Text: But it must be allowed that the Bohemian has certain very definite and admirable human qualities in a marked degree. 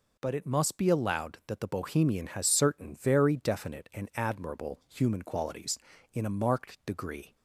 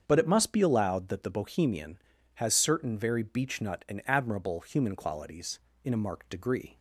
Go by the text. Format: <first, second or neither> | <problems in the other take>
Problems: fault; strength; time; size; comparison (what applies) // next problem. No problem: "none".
first | starts louder than the rest; strong; until 1.0 s; 7.5 dB // says "beechnut" for "definite"; at 3.2 s